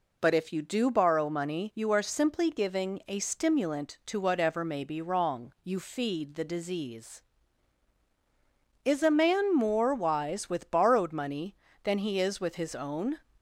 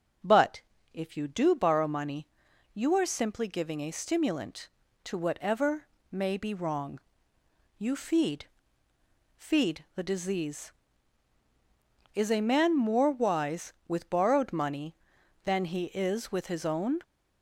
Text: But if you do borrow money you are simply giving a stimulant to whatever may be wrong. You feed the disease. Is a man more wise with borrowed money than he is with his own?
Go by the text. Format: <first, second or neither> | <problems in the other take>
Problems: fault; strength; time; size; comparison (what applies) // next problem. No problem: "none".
first | starts louder than the rest; until 1.5 s; 6.5 dB // pauses between "But" and "if"; slight; at 0.6 s; 0.32 s long // pauses between "money" and "you"; noticeable; at 2.2 s; 0.46 s long // pauses between "whatever" and "may"; slight; at 5.8 s; 0.26 s long // says "feed" twice; at 9.3 s